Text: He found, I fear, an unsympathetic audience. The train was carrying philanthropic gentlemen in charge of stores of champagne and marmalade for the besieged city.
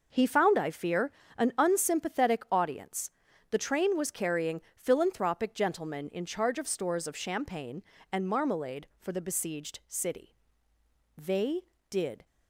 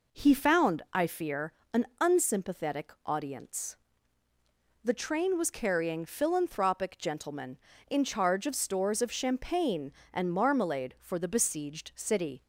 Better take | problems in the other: second | goes on to say "They did"; noticeable; from 11.1 s on; 1.0 s long

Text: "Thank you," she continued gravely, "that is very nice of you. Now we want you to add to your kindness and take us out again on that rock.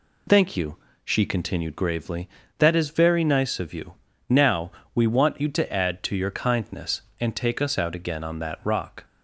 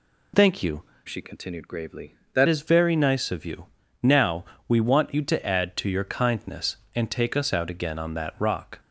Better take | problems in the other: first | changes voice from "she" to "that"; from 1.0 to 2.4 s; 1.4 s long // pauses between "Now" and "we"; slight; at 4.4 s; 0.20 s long; slight in the first

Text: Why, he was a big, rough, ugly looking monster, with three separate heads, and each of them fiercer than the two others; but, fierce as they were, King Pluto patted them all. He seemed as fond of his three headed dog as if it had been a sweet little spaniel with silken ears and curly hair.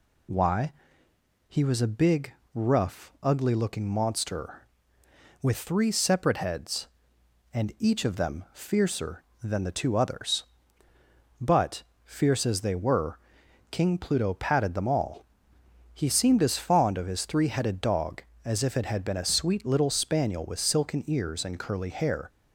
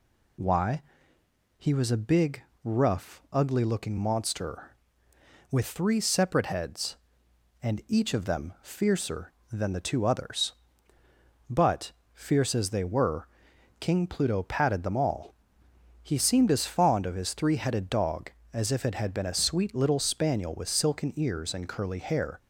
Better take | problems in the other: neither | none

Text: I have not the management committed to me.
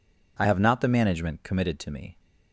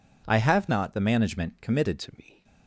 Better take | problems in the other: first | changes voice at "to"; from 1.9 s on; 0.5 s long

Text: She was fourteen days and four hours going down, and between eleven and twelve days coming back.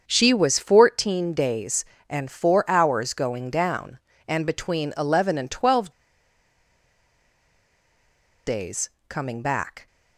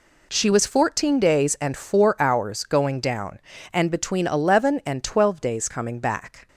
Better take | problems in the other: second | starts louder than the rest; until 1.0 s; 7 dB // pauses between "twelve" and "days"; strong; at 5.9 s; 2.5 s long // pauses between "days" and "coming"; slight; at 8.9 s; 0.18 s long

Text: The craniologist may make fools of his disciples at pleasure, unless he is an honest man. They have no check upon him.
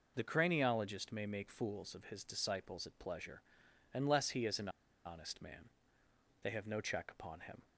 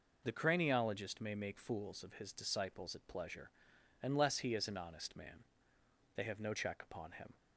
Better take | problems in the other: second | pauses between "an" and "honest"; at 4.6 s; 0.36 s long

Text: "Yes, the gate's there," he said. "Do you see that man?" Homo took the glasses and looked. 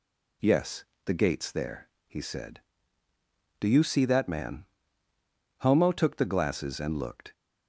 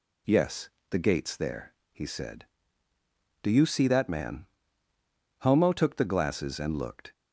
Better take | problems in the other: neither | none

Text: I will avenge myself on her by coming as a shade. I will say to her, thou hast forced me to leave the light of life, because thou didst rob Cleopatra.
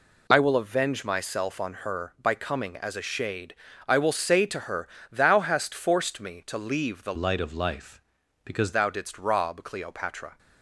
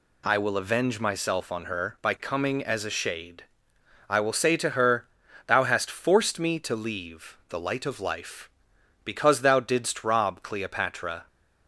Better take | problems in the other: second | changes voice from "light" to "because"; from 7.1 to 8.7 s; 1.6 s long

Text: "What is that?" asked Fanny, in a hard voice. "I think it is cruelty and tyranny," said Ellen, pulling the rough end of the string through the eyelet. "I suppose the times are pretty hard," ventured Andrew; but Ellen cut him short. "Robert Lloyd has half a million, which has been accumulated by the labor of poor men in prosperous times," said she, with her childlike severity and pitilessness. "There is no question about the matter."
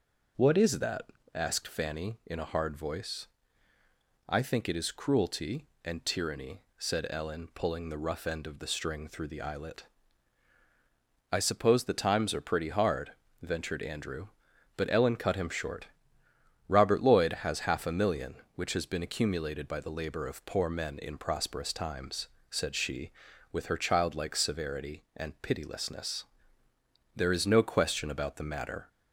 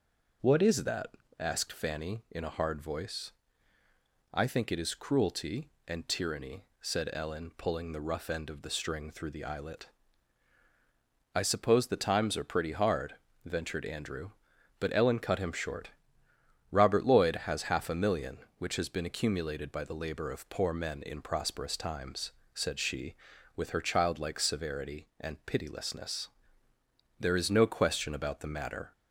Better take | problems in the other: neither | none

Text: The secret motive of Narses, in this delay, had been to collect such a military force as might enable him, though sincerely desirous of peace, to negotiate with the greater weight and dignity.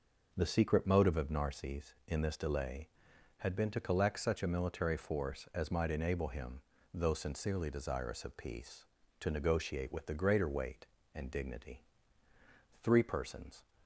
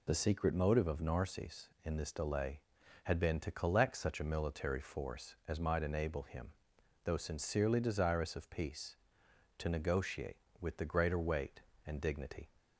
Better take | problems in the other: second | goes on to say "Three persons"; noticeable; from 12.8 s on; 0.82 s long

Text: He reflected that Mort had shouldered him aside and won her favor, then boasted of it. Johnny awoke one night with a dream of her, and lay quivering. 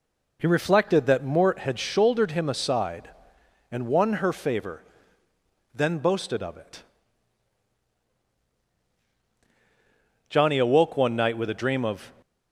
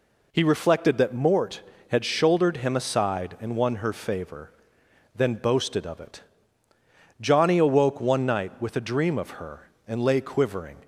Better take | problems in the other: second | stops before "her and lay quivering"; at 12.2 s

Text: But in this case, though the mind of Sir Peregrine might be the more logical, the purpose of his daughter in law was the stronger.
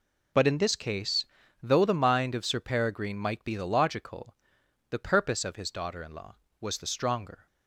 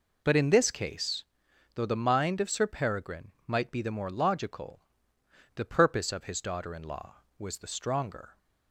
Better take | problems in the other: second | skips "more"; at 3.6 s

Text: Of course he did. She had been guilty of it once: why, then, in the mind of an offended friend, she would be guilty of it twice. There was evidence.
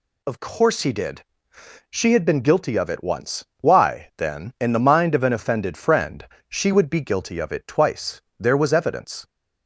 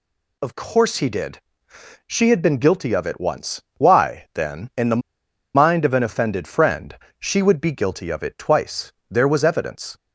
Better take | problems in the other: first | pauses between "the" and "mind"; noticeable; at 5.0 s; 0.56 s long

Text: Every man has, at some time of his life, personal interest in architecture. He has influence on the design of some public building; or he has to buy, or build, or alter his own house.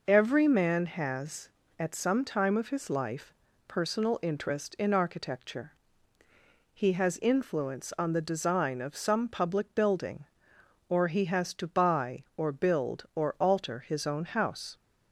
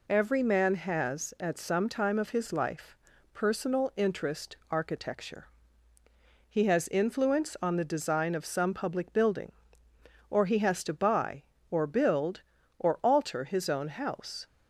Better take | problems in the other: first | skips "in"; at 4.6 s

